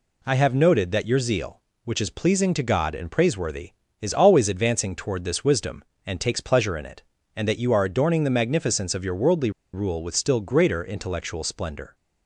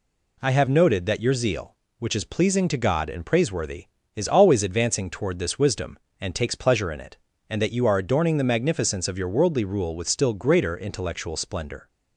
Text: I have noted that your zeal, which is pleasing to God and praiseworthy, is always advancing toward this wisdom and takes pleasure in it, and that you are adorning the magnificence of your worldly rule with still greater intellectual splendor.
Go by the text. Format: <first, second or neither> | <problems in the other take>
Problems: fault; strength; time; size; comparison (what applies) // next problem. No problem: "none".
second | pauses between "worldly" and "rule"; slight; at 9.4 s; 0.23 s long